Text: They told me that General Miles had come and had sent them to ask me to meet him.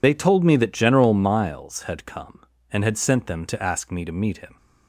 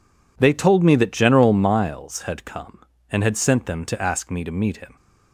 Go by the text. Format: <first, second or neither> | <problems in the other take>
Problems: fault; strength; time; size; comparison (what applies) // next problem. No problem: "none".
second | loses the start of "They"; at 0.0 s; 55 ms